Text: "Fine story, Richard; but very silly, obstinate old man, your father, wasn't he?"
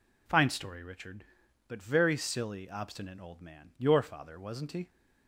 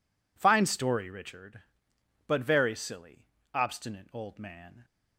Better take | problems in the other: first | stops before "your father wasn't he"; at 4.8 s

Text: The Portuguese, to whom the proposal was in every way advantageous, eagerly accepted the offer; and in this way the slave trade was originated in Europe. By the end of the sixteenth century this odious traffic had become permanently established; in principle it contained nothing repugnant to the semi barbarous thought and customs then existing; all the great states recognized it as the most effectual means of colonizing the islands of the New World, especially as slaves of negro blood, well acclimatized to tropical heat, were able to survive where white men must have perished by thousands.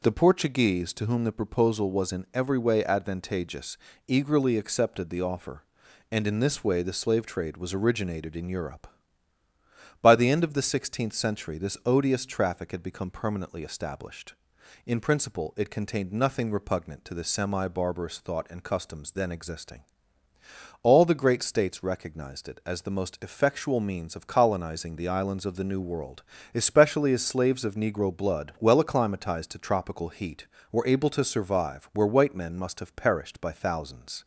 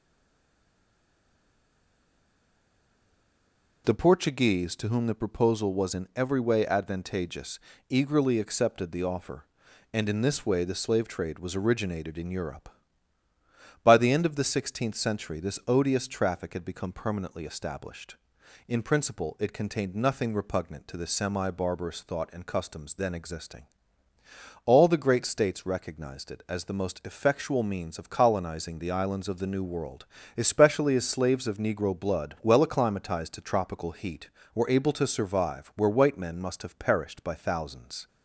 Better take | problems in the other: first | stays silent before the first word; strong; until 3.8 s; 3.8 s long

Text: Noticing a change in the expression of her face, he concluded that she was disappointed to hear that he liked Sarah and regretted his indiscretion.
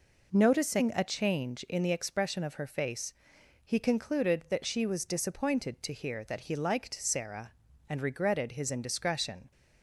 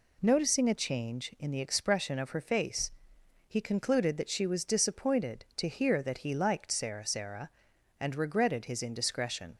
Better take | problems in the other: first | says "Sarah" twice; at 7.0 s

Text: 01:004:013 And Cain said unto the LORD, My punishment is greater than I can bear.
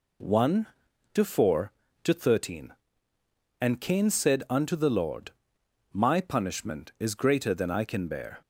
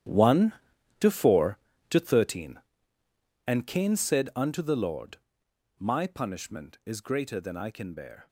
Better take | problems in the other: first | gets quieter; strong; throughout; 15 dB

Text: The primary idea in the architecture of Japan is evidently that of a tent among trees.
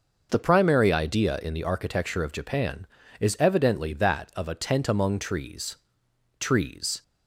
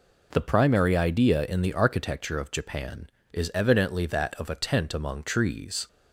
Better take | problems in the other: second | says "trees" twice; at 6.3 s

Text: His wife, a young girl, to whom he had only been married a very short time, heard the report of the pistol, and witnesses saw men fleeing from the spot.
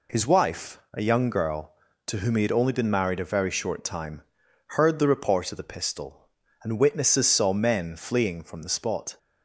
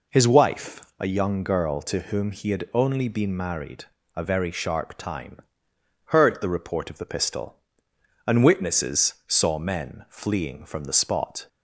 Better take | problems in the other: first | pauses between "married" and "a"; slight; at 3.8 s; 0.34 s long // says "sharp" for "short"; at 4.4 s

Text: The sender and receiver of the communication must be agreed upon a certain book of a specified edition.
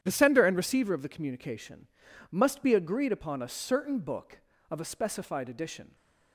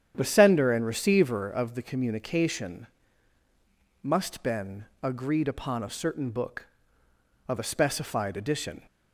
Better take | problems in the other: first | starts louder than the rest; strong; until 1.1 s; 9 dB; strong in the first // pauses between "communication" and "must"; at 2.8 s; 1.1 s long; also in the first // says "been" for "be"; at 4.4 s

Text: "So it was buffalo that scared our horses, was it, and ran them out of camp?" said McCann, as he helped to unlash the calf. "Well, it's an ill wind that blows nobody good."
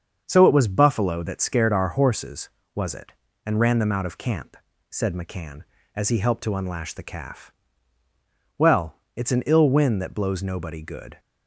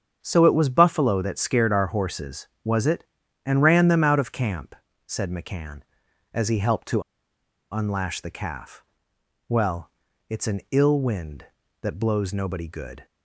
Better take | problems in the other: first | starts louder than the rest; strong; until 1.2 s; 7.5 dB; also in the first // pauses between "to" and "unlash"; noticeable; at 7.0 s; 0.71 s long

